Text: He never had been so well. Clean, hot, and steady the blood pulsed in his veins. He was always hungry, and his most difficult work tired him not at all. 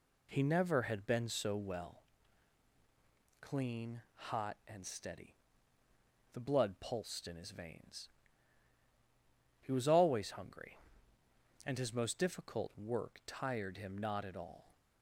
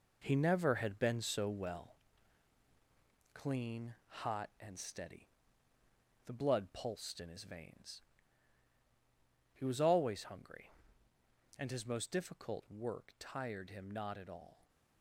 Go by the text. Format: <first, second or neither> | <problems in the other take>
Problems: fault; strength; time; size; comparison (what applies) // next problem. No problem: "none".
first | gets quieter; strong; throughout; 7.5 dB // pauses between "steady" and "the"; noticeable; at 5.2 s; 0.96 s long; noticeable in the first